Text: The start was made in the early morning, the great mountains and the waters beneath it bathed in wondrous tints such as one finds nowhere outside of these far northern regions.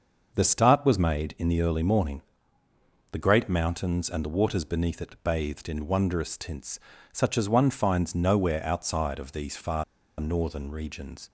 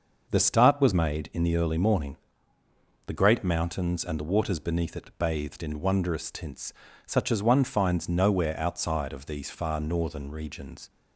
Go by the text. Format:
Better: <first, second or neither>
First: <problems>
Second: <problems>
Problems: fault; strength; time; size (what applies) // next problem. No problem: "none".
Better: second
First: starts louder than the rest; noticeable; until 1.3 s; 6 dB // pauses between "tints" and "such"; slight; at 6.7 s; 0.32 s long // pauses between "far" and "northern"; slight; at 9.8 s; 0.35 s long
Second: pauses between "tints" and "such"; slight; at 6.7 s; 0.32 s long